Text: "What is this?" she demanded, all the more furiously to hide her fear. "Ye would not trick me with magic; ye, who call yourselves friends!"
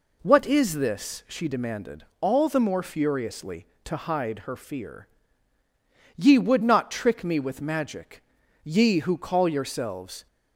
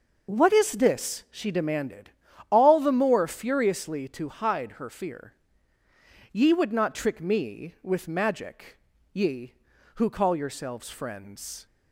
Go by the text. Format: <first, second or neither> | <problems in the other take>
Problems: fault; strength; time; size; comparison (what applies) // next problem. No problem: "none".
second | stops before "friends"; at 10.2 s